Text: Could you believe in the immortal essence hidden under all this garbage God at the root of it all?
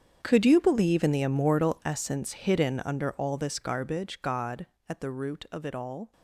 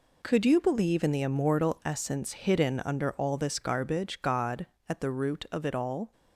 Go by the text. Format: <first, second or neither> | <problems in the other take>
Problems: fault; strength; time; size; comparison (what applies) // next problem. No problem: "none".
second | gets quieter; strong; throughout; 16 dB